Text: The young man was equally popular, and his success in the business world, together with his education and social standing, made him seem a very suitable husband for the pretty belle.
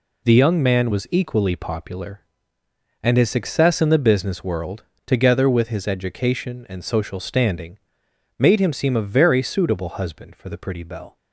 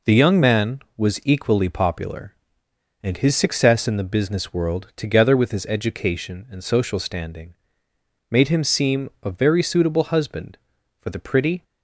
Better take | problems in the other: first | stops before "belle"; at 11.6 s

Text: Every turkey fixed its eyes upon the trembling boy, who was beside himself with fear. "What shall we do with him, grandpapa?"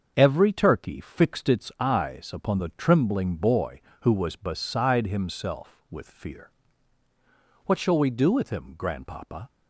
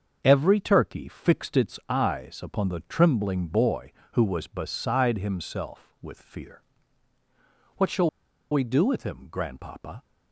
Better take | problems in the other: first | starts louder than the rest; until 1.2 s; 6.5 dB; also in the first // pauses between "shall" and "we"; at 8.0 s; 0.42 s long

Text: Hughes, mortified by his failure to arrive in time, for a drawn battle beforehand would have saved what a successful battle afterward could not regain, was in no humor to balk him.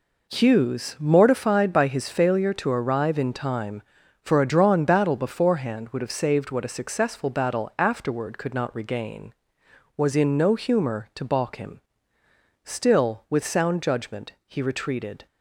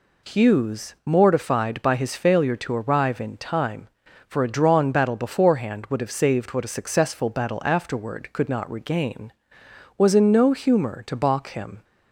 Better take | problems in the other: second | goes on to say "Still with sound judgment he retreated"; strong; from 12.6 s on; 2.6 s long

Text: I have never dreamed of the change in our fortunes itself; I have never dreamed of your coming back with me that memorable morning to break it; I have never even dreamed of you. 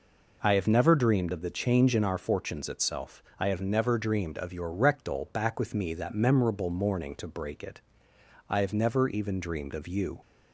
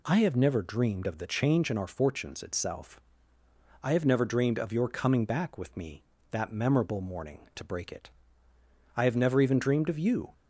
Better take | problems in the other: second | says "rectal" for "coming"; at 4.7 s

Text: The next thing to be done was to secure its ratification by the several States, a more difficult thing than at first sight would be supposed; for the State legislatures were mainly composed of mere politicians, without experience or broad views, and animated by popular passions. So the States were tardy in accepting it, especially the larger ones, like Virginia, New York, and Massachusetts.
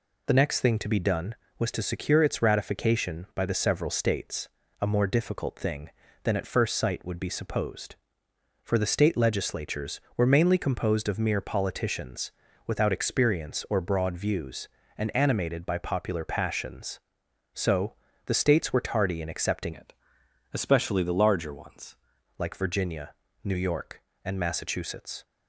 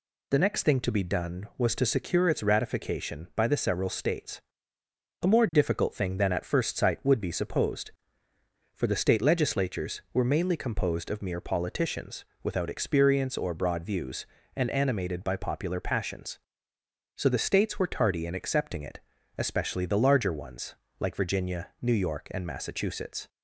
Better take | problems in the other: second | pauses between "So" and "the"; slight; at 17.9 s; 0.30 s long // changes voice from "it" to "ones"; from 19.7 to 21.9 s; 2.2 s long

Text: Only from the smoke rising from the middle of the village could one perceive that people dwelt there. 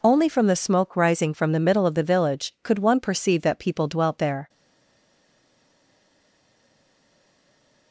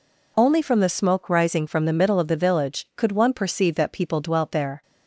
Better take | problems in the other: second | stays silent after the last word; strong; from 4.4 s on; 3.5 s long

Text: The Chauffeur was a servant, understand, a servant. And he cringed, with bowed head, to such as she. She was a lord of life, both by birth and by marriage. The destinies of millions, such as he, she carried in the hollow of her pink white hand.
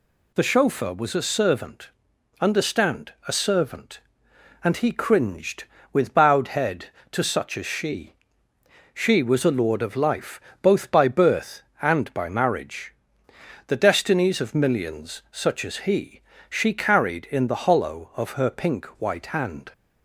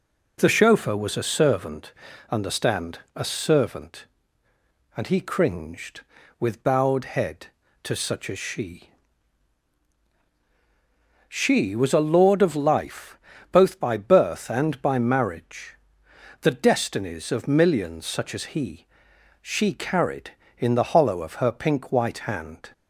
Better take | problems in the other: neither | none

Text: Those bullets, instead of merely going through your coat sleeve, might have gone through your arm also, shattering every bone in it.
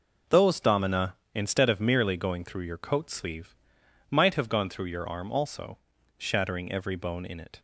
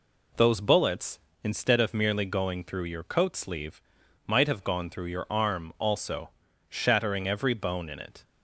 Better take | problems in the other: second | says "domina" for "bullets"; at 0.5 s

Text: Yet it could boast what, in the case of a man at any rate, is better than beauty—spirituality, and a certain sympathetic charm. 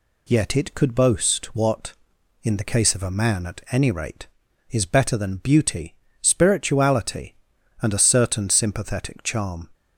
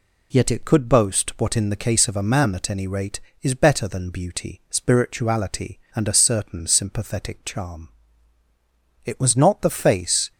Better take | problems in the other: first | goes on to say "It was not the face"; noticeable; from 9.0 s on; 1.2 s long

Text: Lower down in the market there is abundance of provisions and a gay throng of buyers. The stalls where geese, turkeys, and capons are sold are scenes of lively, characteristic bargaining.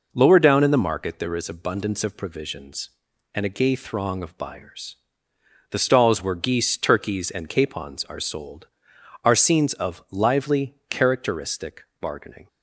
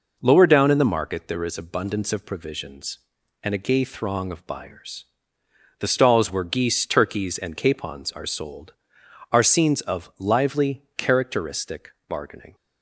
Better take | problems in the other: neither | pauses between "characteristic" and "bargaining"; slight; the same in both

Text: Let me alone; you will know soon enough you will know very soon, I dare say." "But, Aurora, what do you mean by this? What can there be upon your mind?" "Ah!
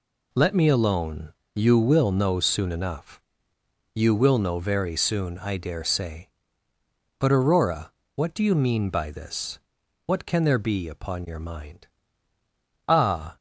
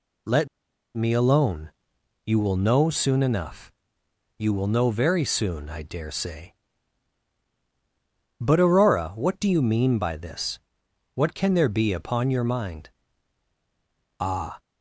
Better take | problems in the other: first | pauses between "Let" and "me"; noticeable; at 0.4 s; 0.49 s long // pauses between "enough" and "you"; noticeable; at 3.7 s; 0.68 s long; noticeable in the first

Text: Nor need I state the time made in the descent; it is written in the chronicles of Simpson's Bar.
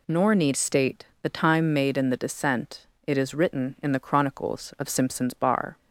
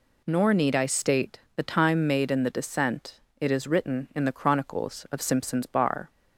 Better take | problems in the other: second | skips "I"; at 0.5 s // pauses between "state" and "the"; slight; at 1.0 s; 0.18 s long; slight in the second

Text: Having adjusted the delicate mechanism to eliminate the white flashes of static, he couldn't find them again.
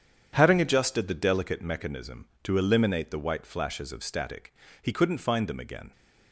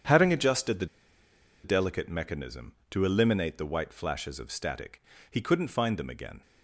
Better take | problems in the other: first | starts louder than the rest; strong; until 1.8 s; 8.5 dB; strong in the first // pauses between "the" and "delicate"; noticeable; at 0.8 s; 0.77 s long

